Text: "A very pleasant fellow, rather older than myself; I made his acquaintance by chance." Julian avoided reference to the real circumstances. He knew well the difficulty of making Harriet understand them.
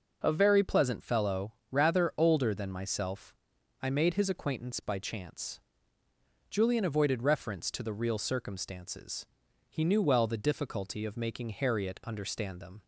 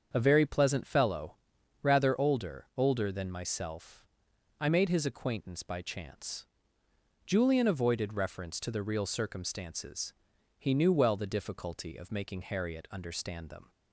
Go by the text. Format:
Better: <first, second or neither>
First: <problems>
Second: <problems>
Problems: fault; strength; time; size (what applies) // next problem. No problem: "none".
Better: first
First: none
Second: starts louder than the rest; strong; until 1.1 s; 7 dB // says "older" twice; at 2.7 s